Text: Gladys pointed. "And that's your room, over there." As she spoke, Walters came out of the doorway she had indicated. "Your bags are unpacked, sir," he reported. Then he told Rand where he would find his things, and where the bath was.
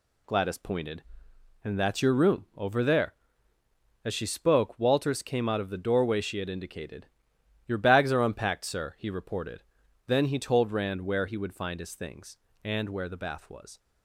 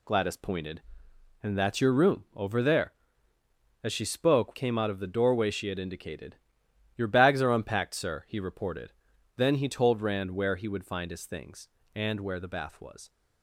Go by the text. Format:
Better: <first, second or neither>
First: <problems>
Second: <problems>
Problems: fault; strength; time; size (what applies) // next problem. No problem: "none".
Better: first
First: none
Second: skips "Walters"; at 4.5 s